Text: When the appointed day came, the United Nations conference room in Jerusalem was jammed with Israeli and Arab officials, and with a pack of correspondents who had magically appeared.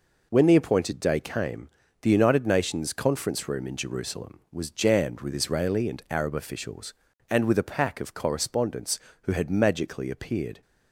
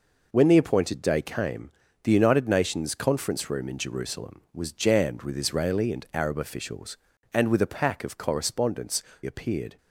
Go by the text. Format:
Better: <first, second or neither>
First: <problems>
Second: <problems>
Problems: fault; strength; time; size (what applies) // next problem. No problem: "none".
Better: first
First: none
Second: skips "who had magically"; at 9.1 s